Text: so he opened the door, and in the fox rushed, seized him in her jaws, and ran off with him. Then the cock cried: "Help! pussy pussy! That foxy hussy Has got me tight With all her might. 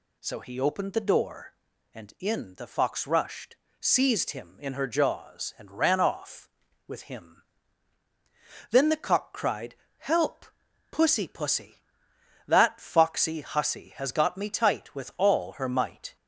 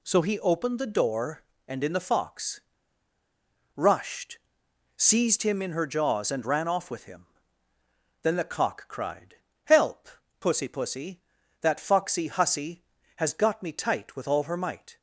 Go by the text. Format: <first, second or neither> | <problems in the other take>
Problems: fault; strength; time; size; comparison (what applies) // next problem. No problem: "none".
first | pauses between "fox" and "rushed"; at 2.6 s; 1.1 s long